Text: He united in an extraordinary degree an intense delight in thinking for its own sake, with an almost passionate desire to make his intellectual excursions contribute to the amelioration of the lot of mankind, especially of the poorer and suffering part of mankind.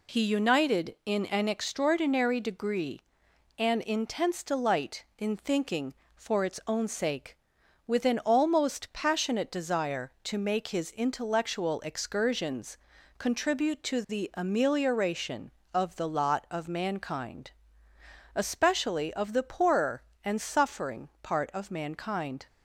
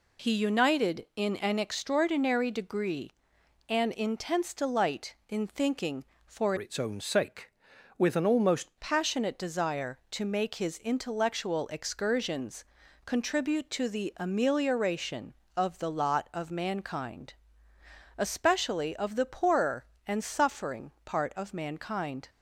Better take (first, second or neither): first